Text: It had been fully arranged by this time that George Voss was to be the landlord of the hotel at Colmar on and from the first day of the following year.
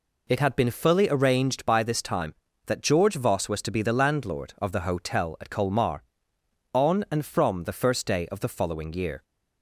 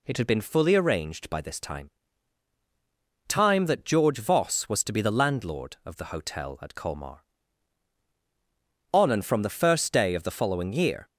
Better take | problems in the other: first | says "time" twice; at 3.2 s

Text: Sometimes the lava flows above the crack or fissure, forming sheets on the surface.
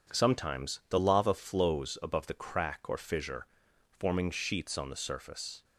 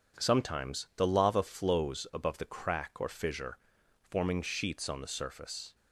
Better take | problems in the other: neither | none

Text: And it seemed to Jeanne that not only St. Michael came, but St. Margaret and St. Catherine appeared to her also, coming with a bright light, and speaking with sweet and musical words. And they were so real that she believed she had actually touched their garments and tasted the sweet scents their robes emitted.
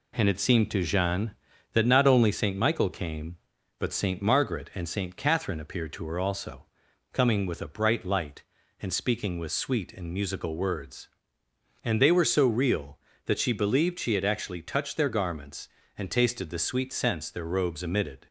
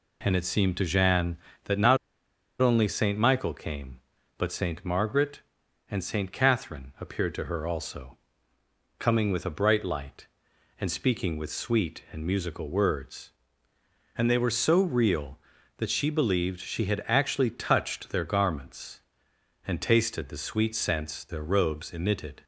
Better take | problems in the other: first | pauses between "not" and "only"; noticeable; at 1.9 s; 0.63 s long

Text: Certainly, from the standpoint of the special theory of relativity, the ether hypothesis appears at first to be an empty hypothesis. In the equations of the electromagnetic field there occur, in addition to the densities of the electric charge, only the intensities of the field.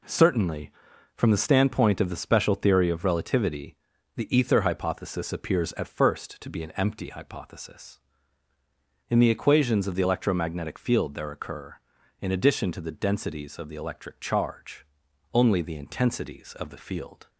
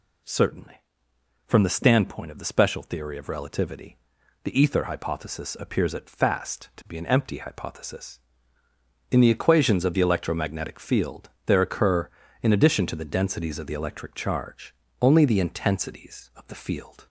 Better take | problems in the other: first | says "fast" for "first"; at 6.0 s // pauses between "field" and "there"; slight; at 11.2 s; 0.18 s long

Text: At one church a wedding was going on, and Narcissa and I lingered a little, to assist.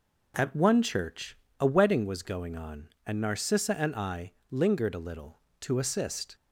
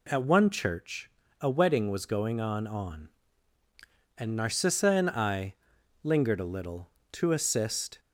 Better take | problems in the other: first | pauses between "church" and "a"; slight; at 1.0 s; 0.32 s long; slight in the first // says "on" twice; at 2.6 s // pauses between "I" and "lingered"; noticeable; at 5.5 s; 0.46 s long; slight in the first

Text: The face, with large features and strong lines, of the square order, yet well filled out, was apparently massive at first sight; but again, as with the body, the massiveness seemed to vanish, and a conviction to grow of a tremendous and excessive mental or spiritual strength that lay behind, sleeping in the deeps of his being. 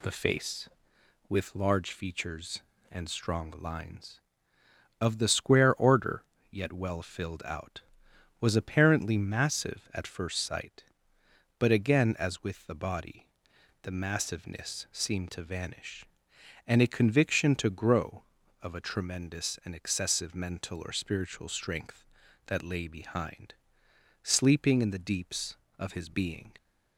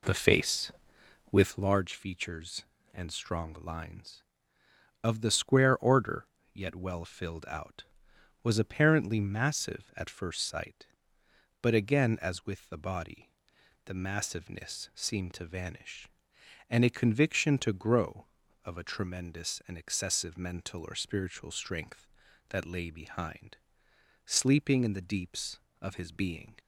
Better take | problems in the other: first | starts louder than the rest; slight; until 1.8 s; 3.5 dB

